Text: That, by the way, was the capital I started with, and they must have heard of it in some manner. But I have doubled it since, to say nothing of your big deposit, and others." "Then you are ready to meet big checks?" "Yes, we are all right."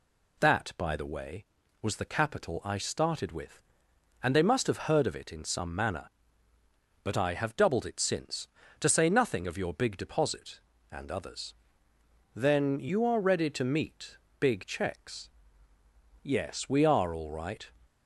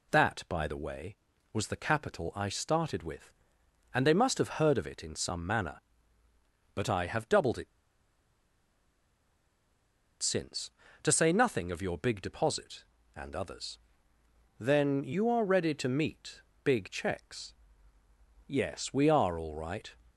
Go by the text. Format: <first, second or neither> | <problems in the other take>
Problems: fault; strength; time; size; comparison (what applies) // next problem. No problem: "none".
first | pauses between "it" and "since"; strong; at 7.6 s; 2.5 s long // pauses between "meet" and "big"; slight; at 16.4 s; 0.24 s long; slight in the first